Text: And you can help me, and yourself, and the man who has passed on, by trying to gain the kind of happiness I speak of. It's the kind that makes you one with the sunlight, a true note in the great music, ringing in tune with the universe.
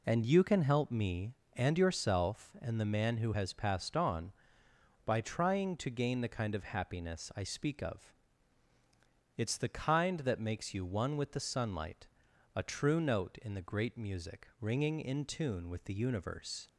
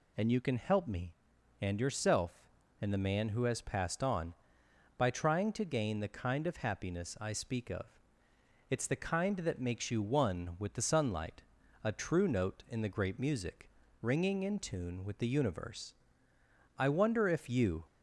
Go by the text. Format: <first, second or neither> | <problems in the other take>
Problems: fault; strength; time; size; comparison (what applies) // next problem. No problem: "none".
first | goes on to say "I wonder if you"; noticeable; from 16.7 s on; 1.0 s long